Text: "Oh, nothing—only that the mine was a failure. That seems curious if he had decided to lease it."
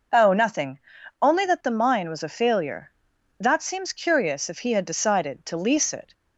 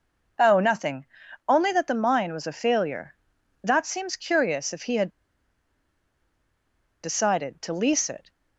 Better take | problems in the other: first | pauses between "had" and "decided"; strong; at 5.0 s; 1.9 s long

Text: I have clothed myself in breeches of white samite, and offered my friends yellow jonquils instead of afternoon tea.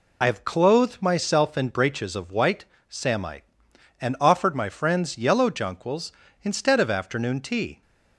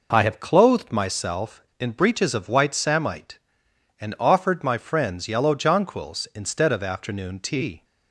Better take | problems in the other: second | loses the start of "I"; at 0.2 s; 50 ms // pauses between "white" and "samite"; slight; at 2.6 s; 0.24 s long

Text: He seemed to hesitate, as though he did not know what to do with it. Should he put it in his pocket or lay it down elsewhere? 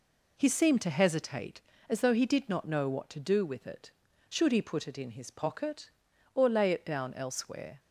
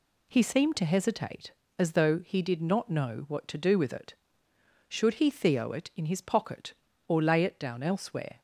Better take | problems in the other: first | says "theo" for "put"; at 5.2 s

